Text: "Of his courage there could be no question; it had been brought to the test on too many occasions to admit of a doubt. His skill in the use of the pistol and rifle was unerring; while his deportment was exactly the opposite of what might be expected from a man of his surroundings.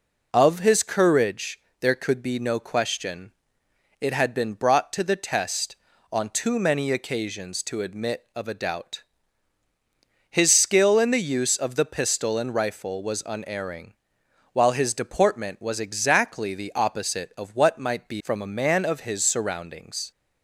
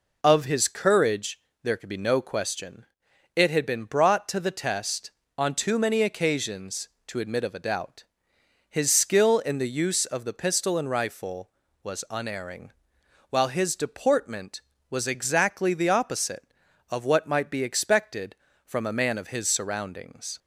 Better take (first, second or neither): second